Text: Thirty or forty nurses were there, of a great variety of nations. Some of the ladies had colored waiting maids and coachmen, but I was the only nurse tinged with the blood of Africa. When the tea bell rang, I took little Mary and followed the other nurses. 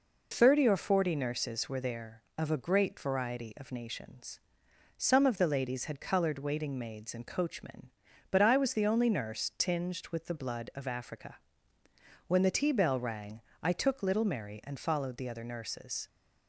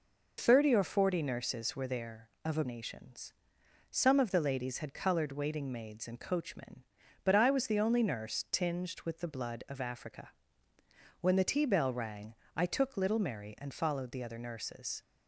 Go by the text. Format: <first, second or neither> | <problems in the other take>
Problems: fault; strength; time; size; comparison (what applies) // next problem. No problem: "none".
first | skips "great variety of"; at 2.6 s